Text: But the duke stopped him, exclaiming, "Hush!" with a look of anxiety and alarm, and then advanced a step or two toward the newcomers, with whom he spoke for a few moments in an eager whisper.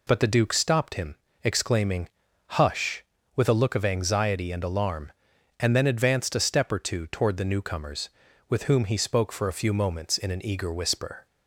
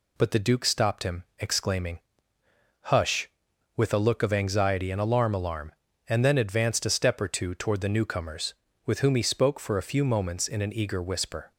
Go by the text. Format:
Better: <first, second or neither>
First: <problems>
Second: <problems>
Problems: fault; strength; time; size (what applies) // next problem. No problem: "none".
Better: first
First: none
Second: says "alarm" twice; at 5.3 s